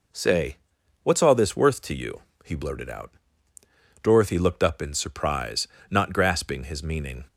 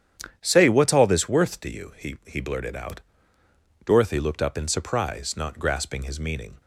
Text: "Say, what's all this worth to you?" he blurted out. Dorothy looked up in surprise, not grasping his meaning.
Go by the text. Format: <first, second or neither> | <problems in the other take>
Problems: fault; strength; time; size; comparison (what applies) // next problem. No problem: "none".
first | starts louder than the rest; strong; until 1.4 s; 9.5 dB // says "he" twice; at 2.2 s